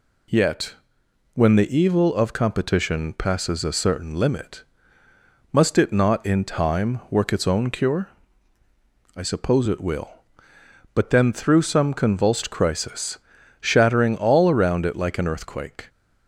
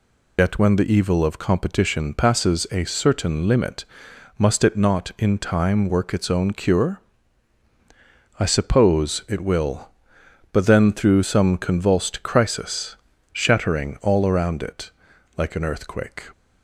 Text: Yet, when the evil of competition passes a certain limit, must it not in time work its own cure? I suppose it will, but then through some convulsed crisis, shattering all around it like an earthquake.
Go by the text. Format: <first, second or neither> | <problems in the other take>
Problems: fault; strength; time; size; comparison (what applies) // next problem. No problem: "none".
first | loses the start of "Yet"; at 0.3 s; 110 ms // pauses between "it" and "like"; noticeable; at 14.8 s; 0.46 s long